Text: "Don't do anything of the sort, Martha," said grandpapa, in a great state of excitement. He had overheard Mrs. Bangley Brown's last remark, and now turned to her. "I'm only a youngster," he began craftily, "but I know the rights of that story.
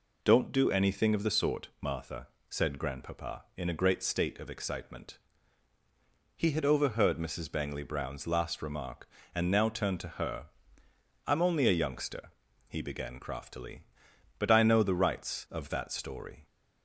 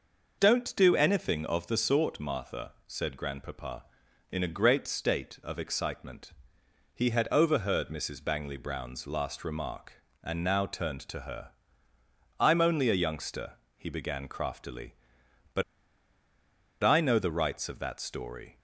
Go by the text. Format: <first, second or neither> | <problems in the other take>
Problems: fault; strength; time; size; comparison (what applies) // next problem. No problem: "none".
first | pauses between "but" and "I"; at 15.6 s; 1.2 s long